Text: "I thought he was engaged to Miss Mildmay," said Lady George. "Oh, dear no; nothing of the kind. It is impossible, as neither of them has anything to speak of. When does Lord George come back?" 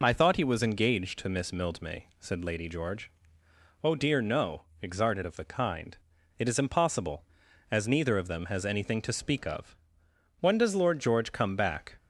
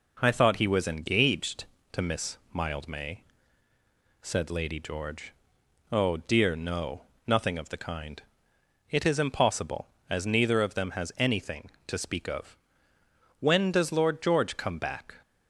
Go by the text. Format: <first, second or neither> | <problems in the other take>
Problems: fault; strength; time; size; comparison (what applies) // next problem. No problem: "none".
second | says "exarted" for "nothing"; at 4.8 s